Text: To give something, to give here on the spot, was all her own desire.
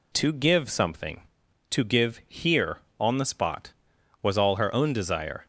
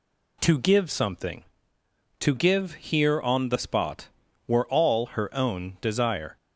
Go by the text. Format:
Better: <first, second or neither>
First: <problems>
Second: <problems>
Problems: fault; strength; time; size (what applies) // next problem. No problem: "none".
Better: first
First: none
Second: says "were" for "was"; at 4.4 s